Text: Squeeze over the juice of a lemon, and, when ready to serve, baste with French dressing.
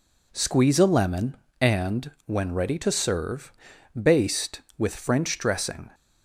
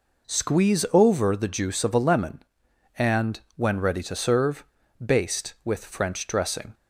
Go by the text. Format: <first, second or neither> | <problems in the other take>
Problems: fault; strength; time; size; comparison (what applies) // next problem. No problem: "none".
second | skips "over the juice of"; at 0.7 s